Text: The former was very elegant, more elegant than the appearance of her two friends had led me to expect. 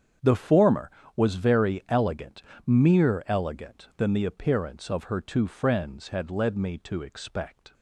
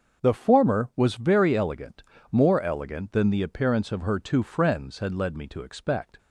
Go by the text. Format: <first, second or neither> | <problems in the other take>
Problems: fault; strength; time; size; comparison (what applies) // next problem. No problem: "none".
second | starts louder than the rest; strong; until 1.4 s; 8 dB; also in the second // says "mere" for "more"; at 2.6 s